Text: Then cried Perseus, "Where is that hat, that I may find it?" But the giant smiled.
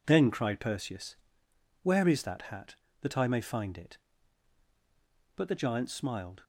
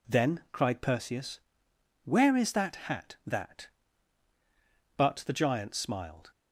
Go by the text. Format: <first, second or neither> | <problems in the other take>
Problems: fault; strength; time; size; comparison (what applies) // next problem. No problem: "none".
first | skips "I may find it"; at 4.3 s